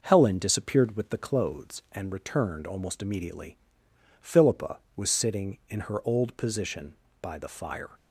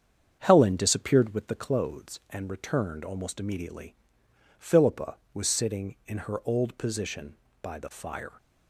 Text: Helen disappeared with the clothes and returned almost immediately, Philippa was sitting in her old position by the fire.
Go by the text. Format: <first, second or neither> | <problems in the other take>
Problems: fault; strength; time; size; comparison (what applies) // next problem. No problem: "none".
first | starts louder than the rest; strong; until 1.5 s; 7.5 dB